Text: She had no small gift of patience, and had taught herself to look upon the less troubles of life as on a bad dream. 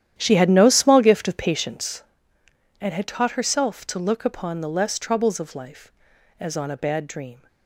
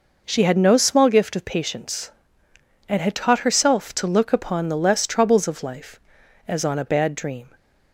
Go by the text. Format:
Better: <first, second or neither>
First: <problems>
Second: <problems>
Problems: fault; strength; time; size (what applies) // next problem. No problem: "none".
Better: second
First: starts louder than the rest; strong; until 2.1 s; 11 dB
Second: none